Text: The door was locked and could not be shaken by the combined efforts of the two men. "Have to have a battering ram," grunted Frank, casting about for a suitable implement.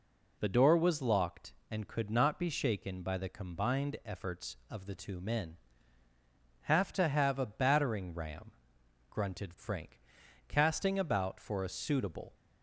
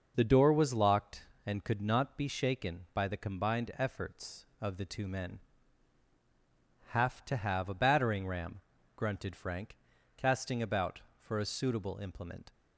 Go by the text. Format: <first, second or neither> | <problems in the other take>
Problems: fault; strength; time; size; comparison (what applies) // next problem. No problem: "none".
second | stops before "implement"; at 12.3 s